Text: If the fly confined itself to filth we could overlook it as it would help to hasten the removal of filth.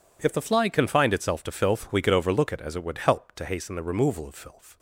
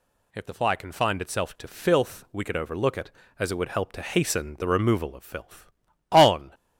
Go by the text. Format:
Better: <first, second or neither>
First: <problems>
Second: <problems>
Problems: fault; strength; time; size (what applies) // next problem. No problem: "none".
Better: first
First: none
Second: goes on to say "On"; slight; from 6.1 s on; 0.42 s long